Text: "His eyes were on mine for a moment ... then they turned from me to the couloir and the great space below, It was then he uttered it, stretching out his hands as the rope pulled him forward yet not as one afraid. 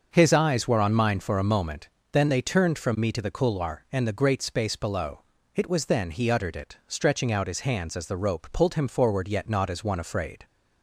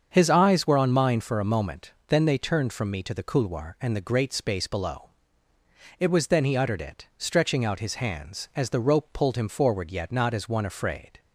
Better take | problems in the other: neither | starts louder than the rest; the same in both

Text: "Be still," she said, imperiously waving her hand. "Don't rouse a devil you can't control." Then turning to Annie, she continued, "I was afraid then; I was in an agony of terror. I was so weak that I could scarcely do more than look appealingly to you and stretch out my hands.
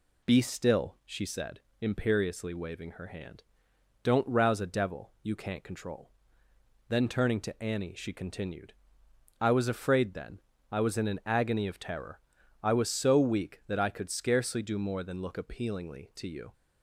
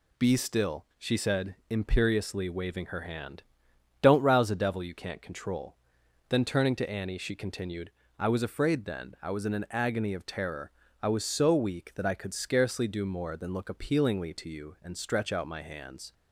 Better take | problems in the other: second | stops before "and stretch out my hands"; at 16.5 s

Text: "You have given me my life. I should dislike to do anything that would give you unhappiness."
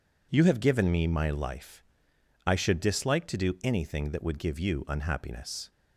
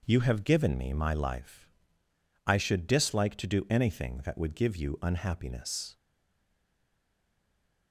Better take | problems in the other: first | stays silent after the last word; noticeable; from 5.9 s on; 2.0 s long

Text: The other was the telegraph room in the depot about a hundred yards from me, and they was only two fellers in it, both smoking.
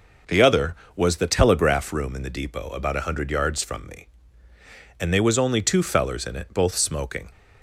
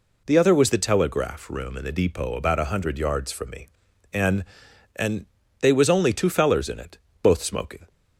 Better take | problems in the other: first | says "and" twice; at 4.9 s

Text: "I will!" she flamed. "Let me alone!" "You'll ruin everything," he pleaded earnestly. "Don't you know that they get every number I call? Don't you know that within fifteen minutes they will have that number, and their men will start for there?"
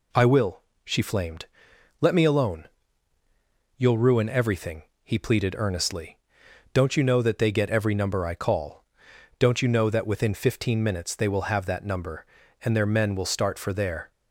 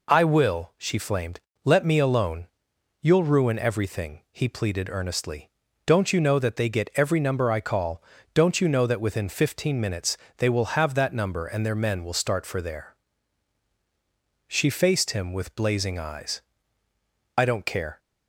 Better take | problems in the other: first | pauses between "minutes" and "they"; slight; at 10.1 s; 0.18 s long // goes on to say "She faced him with blazing eyes I don't care"; strong; from 14.4 s on; 3.5 s long

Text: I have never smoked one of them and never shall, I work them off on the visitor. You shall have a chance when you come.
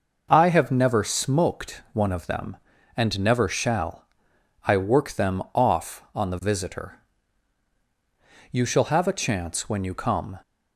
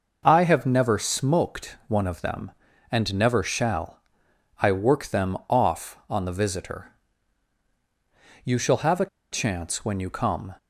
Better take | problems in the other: first | pauses between "a" and "chance"; slight; at 9.0 s; 0.25 s long

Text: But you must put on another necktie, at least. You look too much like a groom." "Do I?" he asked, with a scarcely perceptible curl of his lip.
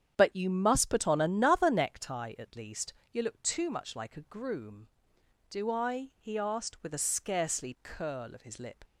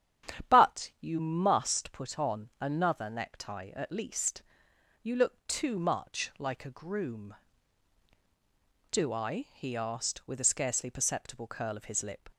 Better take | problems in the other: second | starts louder than the rest; strong; until 1.1 s; 8.5 dB; strong in the second // skips "perceptible"; at 7.7 s

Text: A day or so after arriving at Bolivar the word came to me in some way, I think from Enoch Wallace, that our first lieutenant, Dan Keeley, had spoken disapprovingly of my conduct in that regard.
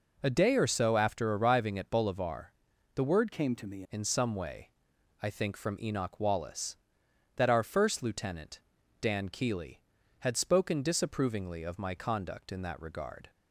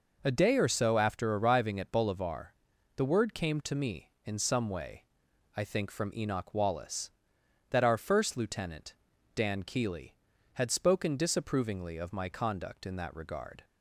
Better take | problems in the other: second | pauses between "Bolivar" and "the"; noticeable; at 2.5 s; 0.46 s long; noticeable in the second // changes voice from "came" to "me"; from 3.3 to 3.8 s; 0.5 s long

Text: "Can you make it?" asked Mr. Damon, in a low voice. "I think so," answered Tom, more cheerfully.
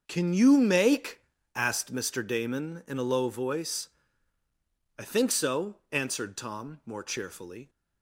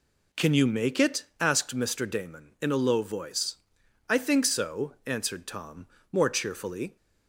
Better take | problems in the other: second | starts louder than the rest; until 1.0 s; 6.5 dB // skips "it"; at 1.3 s

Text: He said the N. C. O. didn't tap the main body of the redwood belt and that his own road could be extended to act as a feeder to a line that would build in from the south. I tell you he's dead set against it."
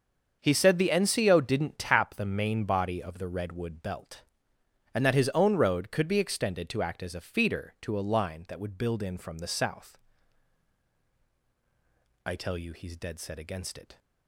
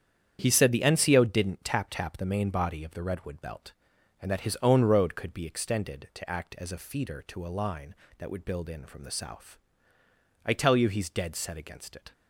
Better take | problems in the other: first | starts louder than the rest; strong; until 1.4 s; 8.5 dB; also in the first // says "tap" twice; at 1.8 s

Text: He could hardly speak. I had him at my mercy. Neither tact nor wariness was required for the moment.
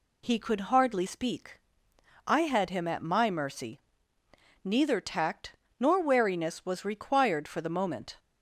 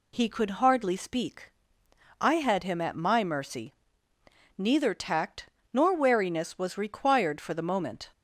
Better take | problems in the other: neither | pauses between "tact" and "nor"; slight; the same in both

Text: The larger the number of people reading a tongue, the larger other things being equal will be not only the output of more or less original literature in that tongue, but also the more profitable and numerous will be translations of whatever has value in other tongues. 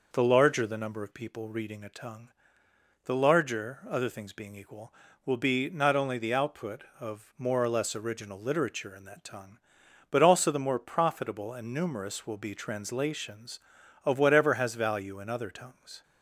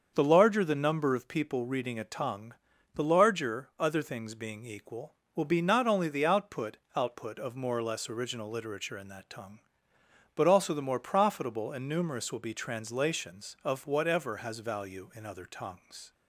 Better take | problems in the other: first | starts louder than the rest; until 1.1 s; 7 dB // says "output" twice; at 6.9 s

